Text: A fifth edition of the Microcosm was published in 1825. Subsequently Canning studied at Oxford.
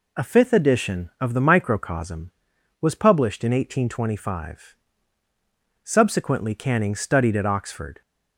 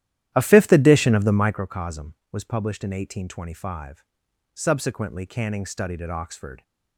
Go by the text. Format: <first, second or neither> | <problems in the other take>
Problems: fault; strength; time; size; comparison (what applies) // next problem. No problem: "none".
first | starts louder than the rest; strong; until 1.7 s; 12 dB